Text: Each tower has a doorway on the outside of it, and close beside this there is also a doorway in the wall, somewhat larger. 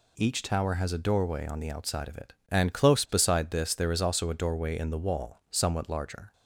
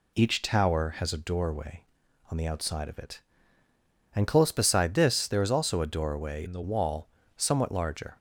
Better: first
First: none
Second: changes voice from "in" to "the"; from 6.4 to 6.6 s; 0.2 s long

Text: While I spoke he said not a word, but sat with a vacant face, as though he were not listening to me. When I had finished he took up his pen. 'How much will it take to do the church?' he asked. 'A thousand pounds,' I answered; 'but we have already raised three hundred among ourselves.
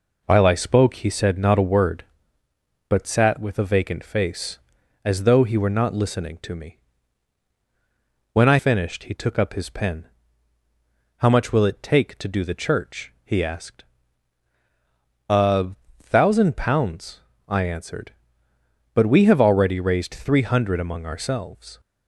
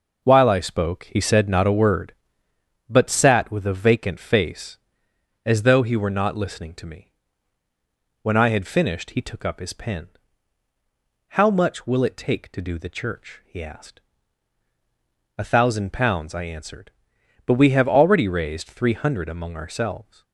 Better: second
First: skips "had"; at 8.5 s // pauses between "A" and "thousand"; slight; at 15.7 s; 0.26 s long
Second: none

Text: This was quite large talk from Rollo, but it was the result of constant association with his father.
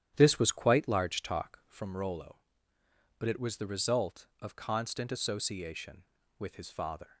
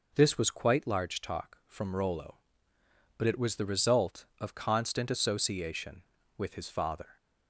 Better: second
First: starts louder than the rest; strong; until 1.8 s; 10.5 dB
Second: none

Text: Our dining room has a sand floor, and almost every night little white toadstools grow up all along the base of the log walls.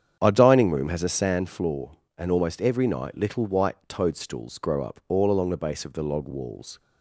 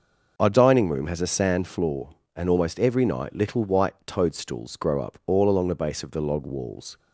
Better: second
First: starts louder than the rest; strong; until 1.2 s; 8.5 dB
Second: none

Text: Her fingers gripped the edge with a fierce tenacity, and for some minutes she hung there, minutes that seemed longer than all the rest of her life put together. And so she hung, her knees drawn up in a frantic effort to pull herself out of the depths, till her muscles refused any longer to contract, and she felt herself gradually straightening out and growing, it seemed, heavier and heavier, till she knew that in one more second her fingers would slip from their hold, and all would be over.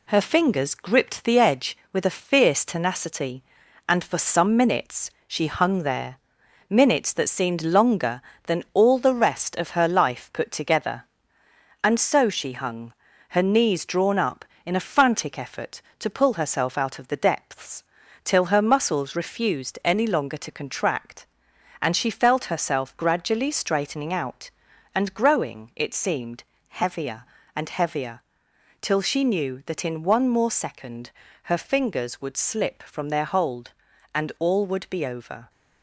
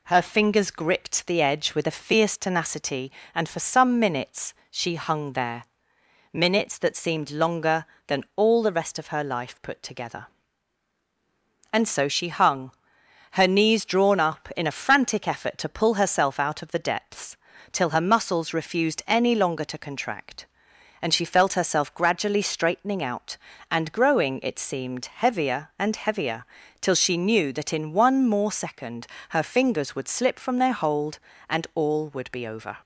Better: second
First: gets quieter; noticeable; throughout; 4 dB // pauses between "minutes" and "she"; slight; at 5.0 s; 0.18 s long // pauses between "second" and "her"; slight; at 31.0 s; 0.34 s long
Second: pauses between "minutes" and "she"; slight; at 4.5 s; 0.16 s long // pauses between "second" and "her"; slight; at 29.0 s; 0.22 s long

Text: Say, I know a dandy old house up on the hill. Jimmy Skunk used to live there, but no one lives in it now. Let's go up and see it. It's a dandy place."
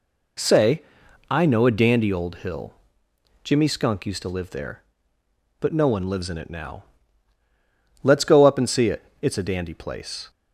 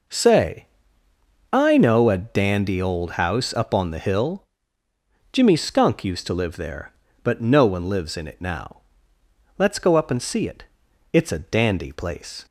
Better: second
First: skips "house up on the"; at 2.3 s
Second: none

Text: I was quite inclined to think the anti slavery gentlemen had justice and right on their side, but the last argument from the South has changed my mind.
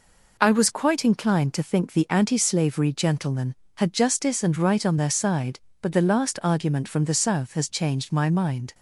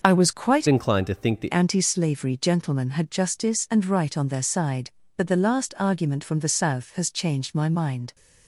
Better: first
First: none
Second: starts louder than the rest; until 1.0 s; 6 dB // changes voice from "inclined" to "the"; from 0.6 to 1.5 s; 0.9 s long

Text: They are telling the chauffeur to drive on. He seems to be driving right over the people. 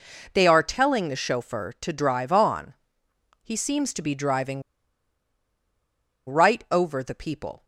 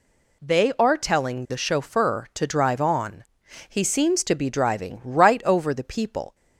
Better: second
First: pauses between "driving" and "right"; strong; at 4.6 s; 1.6 s long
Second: none

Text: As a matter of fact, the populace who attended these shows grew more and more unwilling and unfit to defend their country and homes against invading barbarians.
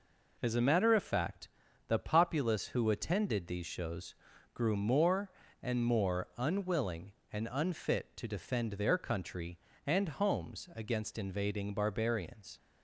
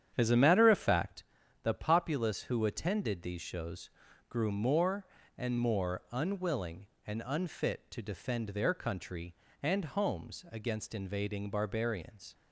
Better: first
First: pauses between "shows" and "grew"; at 4.1 s; 0.40 s long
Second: starts louder than the rest; strong; until 1.2 s; 9 dB // pauses between "shows" and "grew"; at 3.8 s; 0.40 s long

